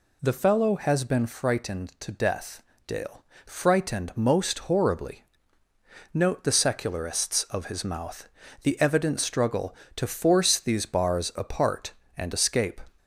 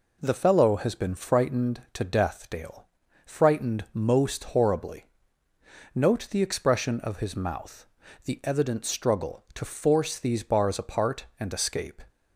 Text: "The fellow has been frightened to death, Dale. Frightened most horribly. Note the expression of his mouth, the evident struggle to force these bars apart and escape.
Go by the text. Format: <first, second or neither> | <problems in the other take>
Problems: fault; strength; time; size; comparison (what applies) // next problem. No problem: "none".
second | says "secularists" for "expression"; at 6.5 s